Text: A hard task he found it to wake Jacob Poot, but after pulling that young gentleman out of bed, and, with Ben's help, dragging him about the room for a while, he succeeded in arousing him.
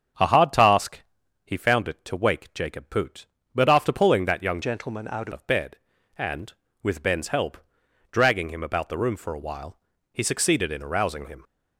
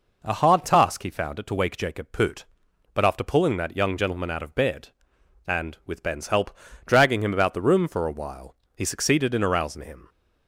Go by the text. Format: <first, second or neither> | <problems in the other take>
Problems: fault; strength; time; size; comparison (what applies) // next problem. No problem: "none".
second | starts louder than the rest; strong; until 1.6 s; 7.5 dB // pauses between "task" and "he"; at 1.0 s; 0.42 s long // changes voice from "gentleman" to "out"; from 4.6 to 5.3 s; 0.7 s long